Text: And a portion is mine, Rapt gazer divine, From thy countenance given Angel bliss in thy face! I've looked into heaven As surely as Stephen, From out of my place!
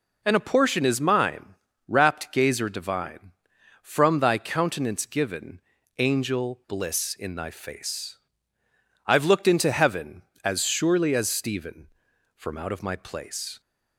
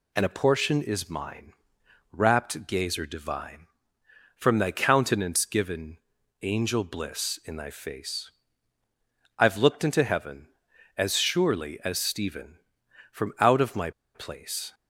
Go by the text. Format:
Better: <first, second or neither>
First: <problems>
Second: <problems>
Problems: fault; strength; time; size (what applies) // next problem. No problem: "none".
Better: first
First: pauses between "given" and "Angel"; at 5.5 s; 0.38 s long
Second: pauses between "given" and "Angel"; at 5.9 s; 0.44 s long // pauses between "my" and "place"; slight; at 13.9 s; 0.24 s long